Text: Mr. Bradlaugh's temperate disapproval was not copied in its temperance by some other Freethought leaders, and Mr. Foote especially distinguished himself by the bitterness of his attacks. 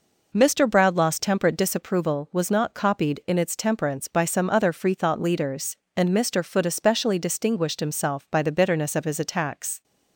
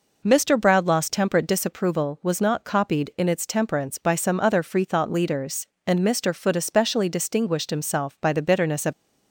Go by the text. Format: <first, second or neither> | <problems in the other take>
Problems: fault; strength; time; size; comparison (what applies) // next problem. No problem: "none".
first | stops before "his attacks"; at 8.9 s